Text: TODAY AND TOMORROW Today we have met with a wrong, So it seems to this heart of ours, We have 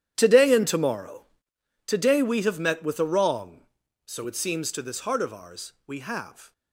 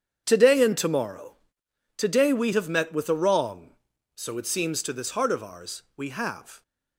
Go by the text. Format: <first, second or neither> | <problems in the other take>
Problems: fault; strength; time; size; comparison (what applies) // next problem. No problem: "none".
second | gets quieter; strong; throughout; 15.5 dB // starts louder than the rest; strong; until 1.1 s; 10.5 dB; strong in the second // pauses between "TOMORROW" and "Today"; noticeable; at 1.2 s; 0.62 s long; noticeable in the second